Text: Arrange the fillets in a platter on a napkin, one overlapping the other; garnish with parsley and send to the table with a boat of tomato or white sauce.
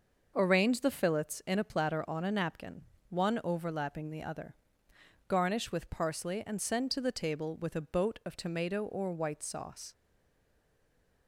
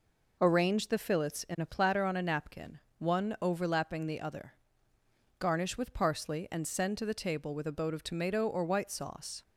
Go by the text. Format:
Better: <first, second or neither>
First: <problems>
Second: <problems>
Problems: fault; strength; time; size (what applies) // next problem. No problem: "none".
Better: second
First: starts louder than the rest; noticeable; until 1.3 s; 6 dB // stays silent after the last word; noticeable; from 9.9 s on; 1.3 s long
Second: none